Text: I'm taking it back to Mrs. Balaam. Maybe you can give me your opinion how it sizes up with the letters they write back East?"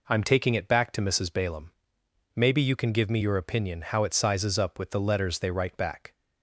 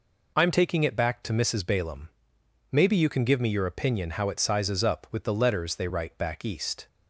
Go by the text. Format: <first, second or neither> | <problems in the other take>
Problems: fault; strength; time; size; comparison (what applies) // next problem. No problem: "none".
second | stops before "East"; at 6.1 s